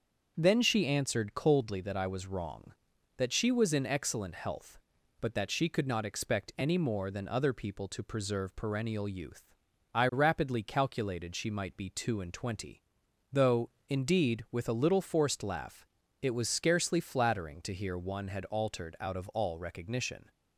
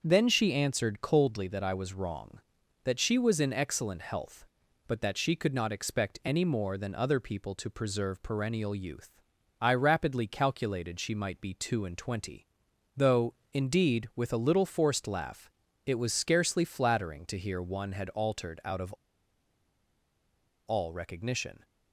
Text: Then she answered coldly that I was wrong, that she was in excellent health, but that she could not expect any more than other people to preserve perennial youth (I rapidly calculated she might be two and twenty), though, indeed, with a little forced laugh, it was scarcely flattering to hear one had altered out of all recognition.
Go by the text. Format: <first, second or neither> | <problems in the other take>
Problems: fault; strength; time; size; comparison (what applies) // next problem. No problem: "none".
first | starts louder than the rest; until 1.0 s; 6.5 dB; also in the first // pauses between "of" and "all"; strong; at 18.9 s; 1.7 s long